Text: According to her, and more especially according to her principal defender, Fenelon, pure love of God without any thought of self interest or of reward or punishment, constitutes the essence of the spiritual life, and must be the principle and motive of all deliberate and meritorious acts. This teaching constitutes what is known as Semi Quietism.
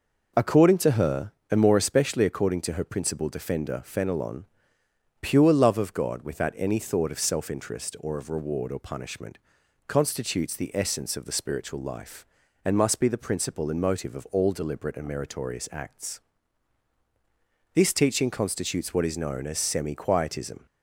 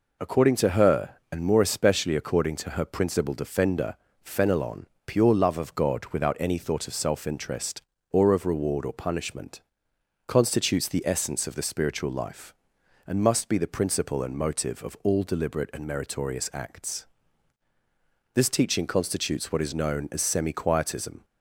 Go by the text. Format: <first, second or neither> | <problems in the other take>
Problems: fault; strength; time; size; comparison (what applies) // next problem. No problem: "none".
neither | none